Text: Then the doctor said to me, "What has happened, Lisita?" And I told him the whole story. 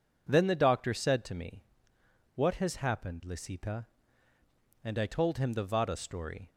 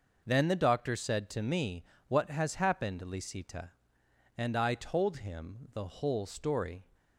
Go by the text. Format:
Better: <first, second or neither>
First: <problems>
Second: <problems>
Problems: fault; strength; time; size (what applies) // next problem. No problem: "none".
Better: second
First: says "vada" for "whole"; at 5.6 s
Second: none